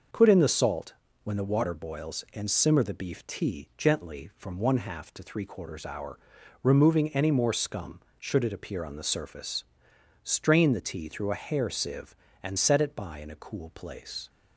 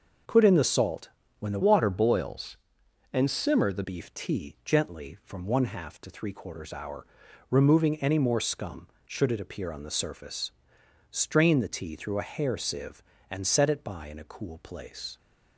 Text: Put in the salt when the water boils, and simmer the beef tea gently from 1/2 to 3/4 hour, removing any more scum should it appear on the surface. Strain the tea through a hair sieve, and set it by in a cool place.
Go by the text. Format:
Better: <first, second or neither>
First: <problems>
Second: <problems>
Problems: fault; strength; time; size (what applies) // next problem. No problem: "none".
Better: first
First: pauses between "salt" and "when"; slight; at 0.9 s; 0.30 s long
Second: pauses between "salt" and "when"; slight; at 1.0 s; 0.30 s long // changes voice from "water" to "the"; from 1.6 to 3.8 s; 2.2 s long